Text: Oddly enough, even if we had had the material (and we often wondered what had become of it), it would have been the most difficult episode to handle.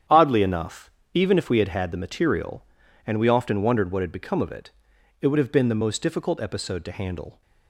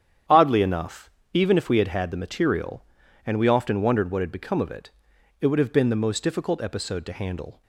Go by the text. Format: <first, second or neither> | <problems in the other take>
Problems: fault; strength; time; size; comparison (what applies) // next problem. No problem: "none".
neither | starts louder than the rest; strong; the same in both